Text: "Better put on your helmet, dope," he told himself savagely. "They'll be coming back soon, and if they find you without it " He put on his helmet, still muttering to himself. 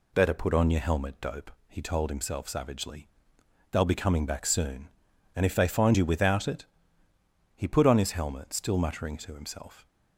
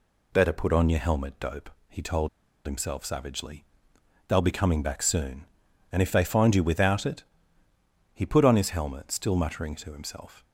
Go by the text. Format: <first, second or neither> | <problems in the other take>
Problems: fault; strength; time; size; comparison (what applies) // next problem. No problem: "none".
first | pauses between "told" and "himself"; at 2.2 s; 0.36 s long